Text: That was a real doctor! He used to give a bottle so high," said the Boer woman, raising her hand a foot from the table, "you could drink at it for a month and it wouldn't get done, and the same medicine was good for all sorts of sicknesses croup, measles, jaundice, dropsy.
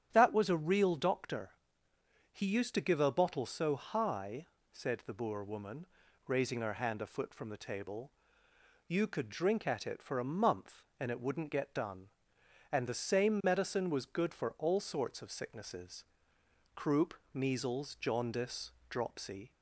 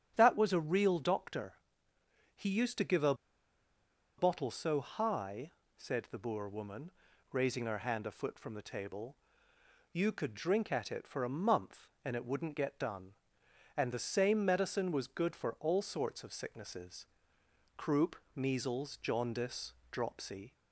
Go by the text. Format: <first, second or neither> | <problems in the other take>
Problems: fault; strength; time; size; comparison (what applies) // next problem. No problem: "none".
first | starts louder than the rest; strong; until 1.1 s; 9 dB; strong in the first // pauses between "a" and "bottle"; at 3.1 s; 1.0 s long // pauses between "sicknesses" and "croup"; noticeable; at 17.0 s; 0.72 s long; noticeable in the first